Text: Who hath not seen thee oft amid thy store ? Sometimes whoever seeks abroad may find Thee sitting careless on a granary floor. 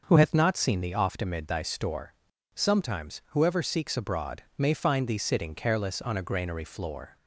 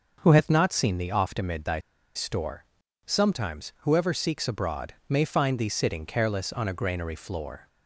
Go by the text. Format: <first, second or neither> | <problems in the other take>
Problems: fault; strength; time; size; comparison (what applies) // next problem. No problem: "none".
first | starts louder than the rest; until 1.2 s; 6 dB; noticeable in the first // pauses between "thy" and "store"; at 1.7 s; 0.36 s long // pauses between "abroad" and "may"; slight; at 4.9 s; 0.16 s long; slight in the first